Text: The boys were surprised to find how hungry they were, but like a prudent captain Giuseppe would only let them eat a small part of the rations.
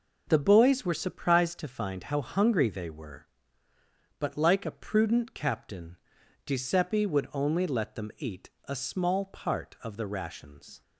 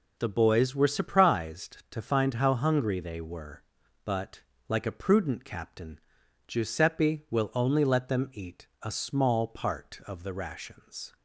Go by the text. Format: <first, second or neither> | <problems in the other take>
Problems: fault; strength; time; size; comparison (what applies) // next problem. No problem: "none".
first | pauses between "but" and "like"; slight; at 4.4 s; 0.26 s long // pauses between "captain" and "Giuseppe"; noticeable; at 5.9 s; 0.48 s long; noticeable in the first // says "will" for "would"; at 7.2 s